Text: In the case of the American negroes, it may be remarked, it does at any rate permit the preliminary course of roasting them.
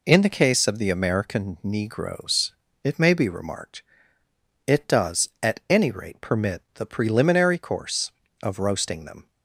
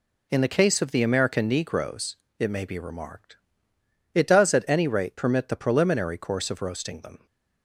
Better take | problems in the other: neither | none

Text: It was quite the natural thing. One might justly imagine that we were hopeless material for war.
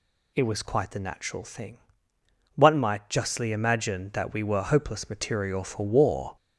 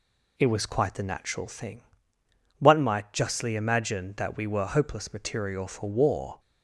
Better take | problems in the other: second | gets louder; noticeable; throughout; 4.5 dB

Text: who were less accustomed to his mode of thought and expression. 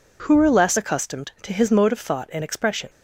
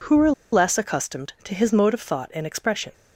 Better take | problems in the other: first | pauses between "were" and "less"; slight; at 0.3 s; 0.20 s long

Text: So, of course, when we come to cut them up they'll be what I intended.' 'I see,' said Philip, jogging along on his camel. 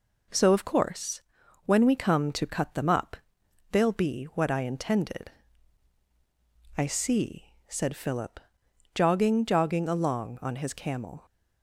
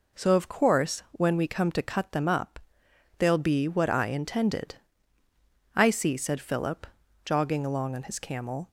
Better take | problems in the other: second | pauses between "up" and "they'll"; noticeable; at 3.1 s; 0.54 s long; noticeable in the second // says "jogging" twice; at 9.4 s

